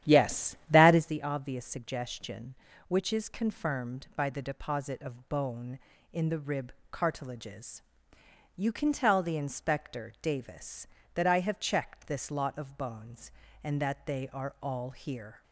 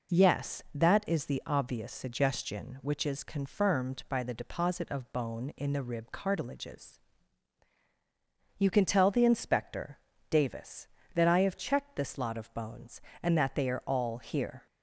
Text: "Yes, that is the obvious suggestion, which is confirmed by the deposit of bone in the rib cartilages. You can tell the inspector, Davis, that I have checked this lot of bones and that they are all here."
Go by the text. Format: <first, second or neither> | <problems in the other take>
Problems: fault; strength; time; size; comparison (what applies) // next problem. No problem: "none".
second | starts louder than the rest; strong; until 1.1 s; 11 dB // pauses between "rib" and "cartilages"; slight; at 6.7 s; 0.18 s long